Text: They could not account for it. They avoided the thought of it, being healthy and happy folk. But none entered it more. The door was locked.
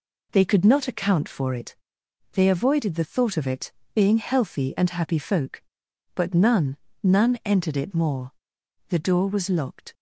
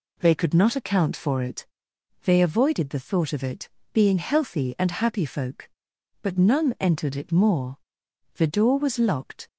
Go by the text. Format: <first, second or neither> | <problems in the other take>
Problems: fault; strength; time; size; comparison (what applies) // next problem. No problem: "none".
second | says "none" twice; at 7.0 s